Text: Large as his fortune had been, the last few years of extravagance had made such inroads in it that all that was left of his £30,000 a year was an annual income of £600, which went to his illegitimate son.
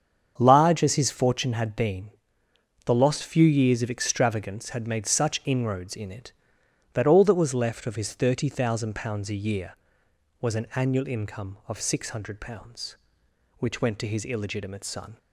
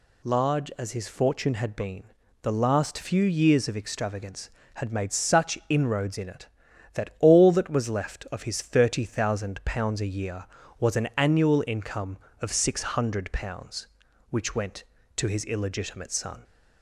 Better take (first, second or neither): second